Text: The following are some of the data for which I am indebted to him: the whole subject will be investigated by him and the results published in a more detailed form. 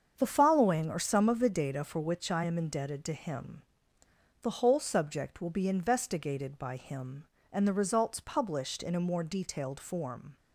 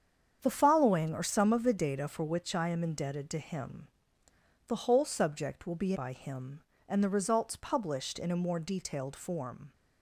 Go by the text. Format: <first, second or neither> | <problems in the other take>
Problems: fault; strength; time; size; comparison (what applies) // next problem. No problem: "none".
first | starts louder than the rest; strong; until 1.4 s; 8 dB; strong in the first // skips "investigated"; at 5.9 s